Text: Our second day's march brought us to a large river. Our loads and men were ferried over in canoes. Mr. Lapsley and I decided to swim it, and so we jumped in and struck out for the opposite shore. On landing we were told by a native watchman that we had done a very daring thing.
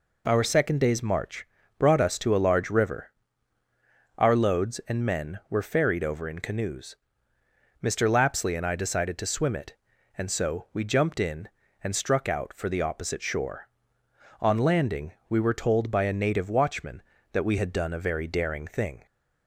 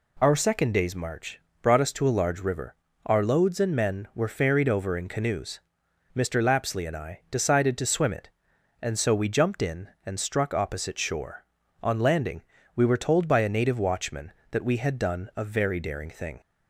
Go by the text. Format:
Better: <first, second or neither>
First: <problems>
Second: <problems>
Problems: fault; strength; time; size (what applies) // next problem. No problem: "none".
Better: first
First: pauses between "march" and "brought"; slight; at 1.4 s; 0.32 s long // pauses between "landing" and "we"; slight; at 15.1 s; 0.16 s long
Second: pauses between "march" and "brought"; slight; at 1.3 s; 0.22 s long // skips "out for the"; at 10.5 s // pauses between "landing" and "we"; slight; at 12.4 s; 0.34 s long